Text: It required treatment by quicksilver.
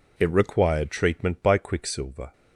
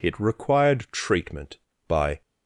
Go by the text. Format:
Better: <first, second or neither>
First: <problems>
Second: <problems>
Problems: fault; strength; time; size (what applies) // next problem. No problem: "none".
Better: first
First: none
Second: stops before "quicksilver"; at 2.2 s